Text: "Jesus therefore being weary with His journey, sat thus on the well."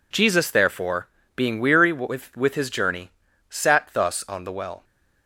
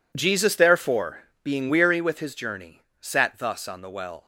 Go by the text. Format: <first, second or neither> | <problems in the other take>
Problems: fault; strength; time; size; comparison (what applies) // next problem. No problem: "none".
second | pauses between "therefore" and "being"; slight; at 1.0 s; 0.28 s long; slight in the second // says "with" twice; at 2.3 s